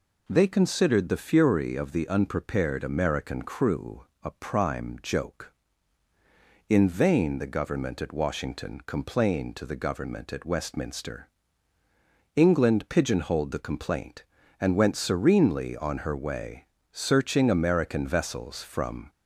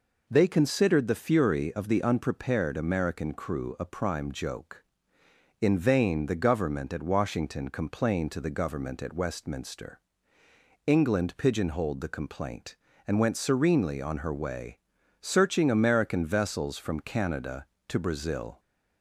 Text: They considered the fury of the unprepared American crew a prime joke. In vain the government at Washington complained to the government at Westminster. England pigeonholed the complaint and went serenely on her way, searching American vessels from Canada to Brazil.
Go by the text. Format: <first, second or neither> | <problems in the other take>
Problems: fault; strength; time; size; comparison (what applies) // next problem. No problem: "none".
second | pauses between "crew" and "a"; slight; at 4.0 s; 0.18 s long // stops before "Canada to Brazil"; at 19.0 s